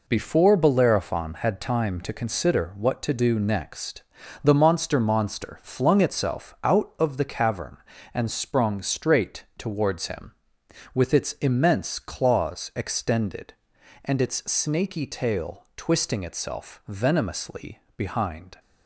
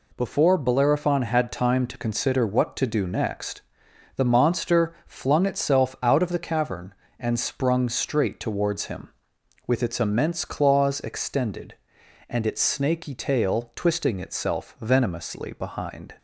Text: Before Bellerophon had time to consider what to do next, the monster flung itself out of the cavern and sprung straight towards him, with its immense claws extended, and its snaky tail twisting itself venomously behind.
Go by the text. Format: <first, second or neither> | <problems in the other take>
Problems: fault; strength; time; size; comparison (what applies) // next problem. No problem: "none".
second | says "monster" twice; at 5.0 s // pauses between "venomously" and "behind"; slight; at 17.8 s; 0.16 s long